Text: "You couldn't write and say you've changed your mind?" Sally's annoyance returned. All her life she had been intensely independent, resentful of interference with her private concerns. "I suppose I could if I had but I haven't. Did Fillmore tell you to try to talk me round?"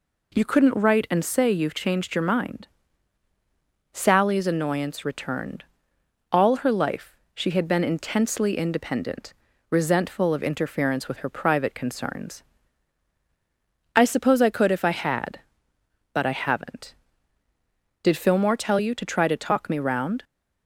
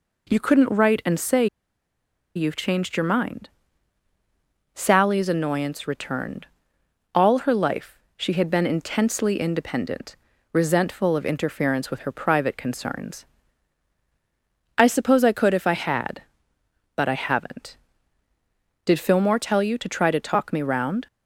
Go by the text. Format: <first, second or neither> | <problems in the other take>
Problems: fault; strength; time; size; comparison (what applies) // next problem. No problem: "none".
first | pauses between "say" and "you've"; noticeable; at 1.4 s; 0.89 s long // pauses between "life" and "she"; slight; at 7.9 s; 0.18 s long; slight in the first